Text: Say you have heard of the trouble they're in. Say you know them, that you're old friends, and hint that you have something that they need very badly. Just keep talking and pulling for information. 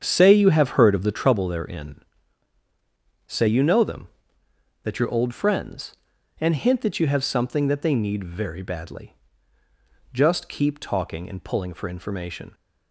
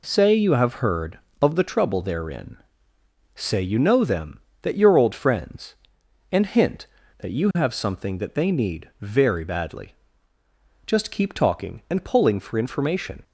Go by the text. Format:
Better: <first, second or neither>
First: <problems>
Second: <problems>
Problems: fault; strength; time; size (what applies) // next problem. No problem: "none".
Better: second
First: starts louder than the rest; strong; until 1.4 s; 7.5 dB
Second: none